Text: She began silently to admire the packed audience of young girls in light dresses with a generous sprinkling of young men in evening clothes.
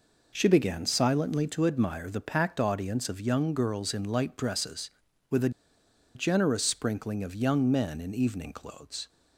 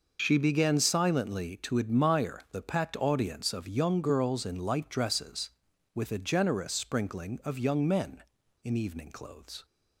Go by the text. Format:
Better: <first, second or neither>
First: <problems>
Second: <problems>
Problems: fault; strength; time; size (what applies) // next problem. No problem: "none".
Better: second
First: pauses between "a" and "generous"; noticeable; at 5.4 s; 0.65 s long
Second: none